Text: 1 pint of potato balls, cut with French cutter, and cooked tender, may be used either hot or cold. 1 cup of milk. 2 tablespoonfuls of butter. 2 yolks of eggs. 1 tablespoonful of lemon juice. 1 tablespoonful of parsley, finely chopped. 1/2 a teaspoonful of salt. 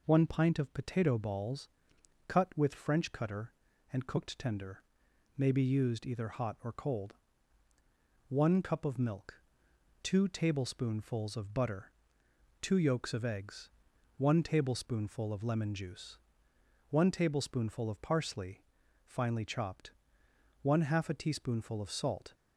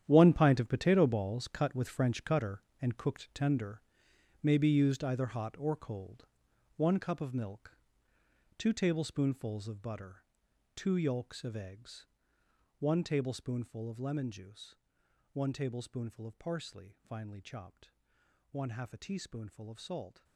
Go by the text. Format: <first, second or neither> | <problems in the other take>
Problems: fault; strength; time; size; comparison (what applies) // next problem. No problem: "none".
first | gets quieter; strong; throughout; 13.5 dB